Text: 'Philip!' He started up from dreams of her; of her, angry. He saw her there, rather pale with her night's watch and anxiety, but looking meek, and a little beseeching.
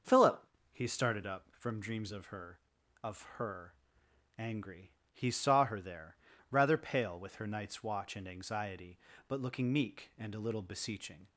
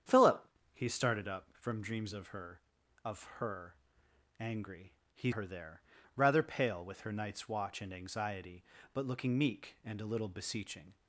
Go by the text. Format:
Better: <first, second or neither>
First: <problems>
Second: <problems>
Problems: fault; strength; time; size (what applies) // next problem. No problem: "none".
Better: first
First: starts louder than the rest; noticeable; until 1.3 s; 6 dB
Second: starts louder than the rest; strong; until 1.3 s; 8.5 dB // skips "saw"; at 5.3 s